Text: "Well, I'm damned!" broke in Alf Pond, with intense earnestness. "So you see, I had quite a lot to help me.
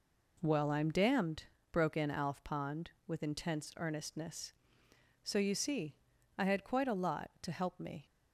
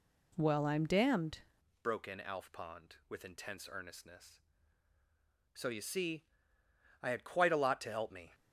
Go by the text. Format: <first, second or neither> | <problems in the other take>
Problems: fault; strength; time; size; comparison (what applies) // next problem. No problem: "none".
first | changes voice at "broke"; from 1.8 s on; 6.5 s long